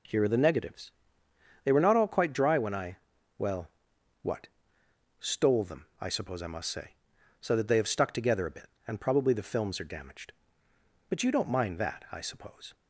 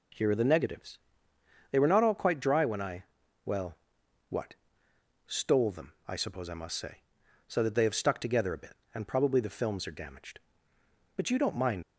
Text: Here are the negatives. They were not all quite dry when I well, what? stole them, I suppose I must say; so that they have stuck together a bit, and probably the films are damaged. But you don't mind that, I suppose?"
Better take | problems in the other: first | pauses between "I" and "well"; at 3.0 s; 0.42 s long; also in the first // stops before "that I suppose"; at 11.8 s

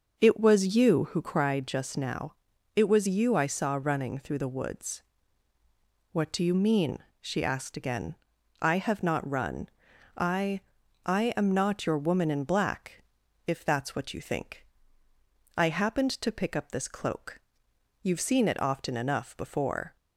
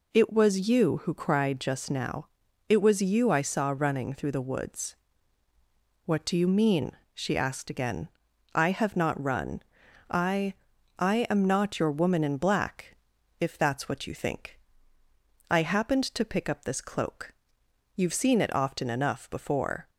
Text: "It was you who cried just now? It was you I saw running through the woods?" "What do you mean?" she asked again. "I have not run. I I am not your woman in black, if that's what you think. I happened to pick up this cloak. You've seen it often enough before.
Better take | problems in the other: second | starts louder than the rest; noticeable; until 1.4 s; 6 dB // pauses between "I" and "I"; at 10.5 s; 0.44 s long; also in the second

